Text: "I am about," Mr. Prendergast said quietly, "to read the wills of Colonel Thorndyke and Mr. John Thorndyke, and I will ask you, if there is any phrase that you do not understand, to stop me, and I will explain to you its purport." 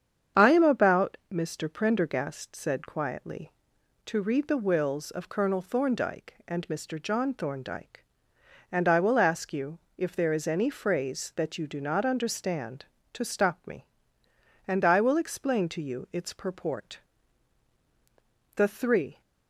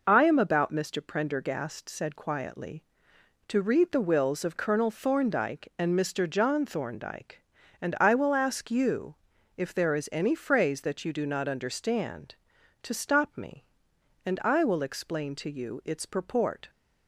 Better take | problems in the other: second | starts louder than the rest; strong; until 1.4 s; 8 dB // goes on to say "The three"; noticeable; from 18.5 s on; 0.66 s long

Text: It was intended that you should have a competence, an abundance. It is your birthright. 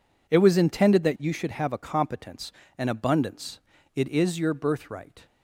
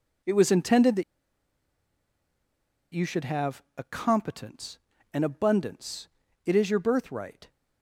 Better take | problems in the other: first | pauses between "that" and "you"; strong; at 1.0 s; 1.9 s long

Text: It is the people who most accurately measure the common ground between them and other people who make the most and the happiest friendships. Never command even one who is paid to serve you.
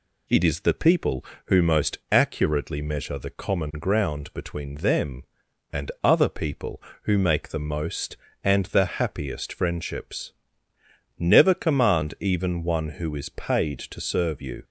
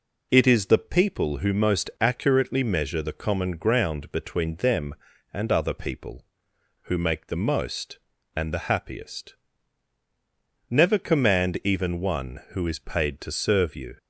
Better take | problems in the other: first | skips "friendships"; at 10.0 s

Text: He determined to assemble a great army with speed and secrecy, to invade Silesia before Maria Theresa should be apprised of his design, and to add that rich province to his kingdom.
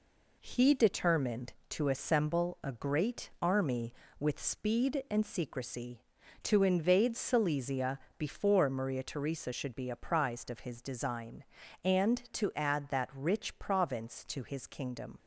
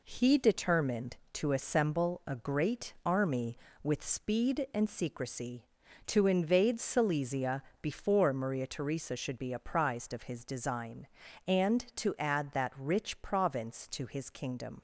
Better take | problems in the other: neither | pauses between "Silesia" and "before"; slight; the same in both

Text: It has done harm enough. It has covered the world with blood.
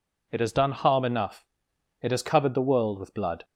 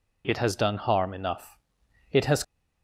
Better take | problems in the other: first | stops before "covered the world with blood"; at 2.4 s

